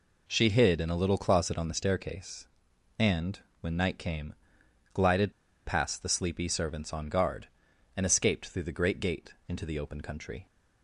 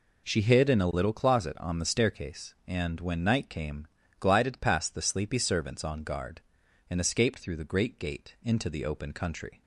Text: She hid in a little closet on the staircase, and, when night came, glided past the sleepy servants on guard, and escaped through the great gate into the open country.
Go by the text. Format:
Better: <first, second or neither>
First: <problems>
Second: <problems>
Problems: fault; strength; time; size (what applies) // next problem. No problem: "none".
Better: second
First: pauses between "glided" and "past"; slight; at 5.3 s; 0.33 s long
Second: none